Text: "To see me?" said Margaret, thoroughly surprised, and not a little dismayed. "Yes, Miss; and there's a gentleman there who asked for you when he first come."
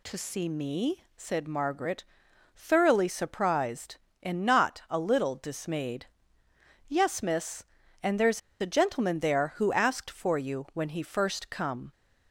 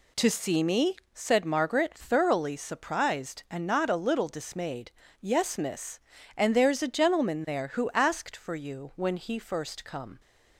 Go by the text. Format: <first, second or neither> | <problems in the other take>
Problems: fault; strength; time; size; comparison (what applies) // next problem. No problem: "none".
second | pauses between "there's" and "a"; slight; at 8.4 s; 0.21 s long